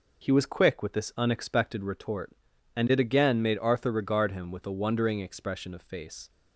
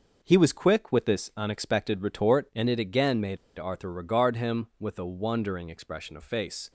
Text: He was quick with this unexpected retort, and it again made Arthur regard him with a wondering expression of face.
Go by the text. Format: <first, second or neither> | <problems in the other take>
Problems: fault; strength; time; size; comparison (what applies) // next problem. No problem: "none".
first | pauses between "made" and "Arthur"; slight; at 3.3 s; 0.21 s long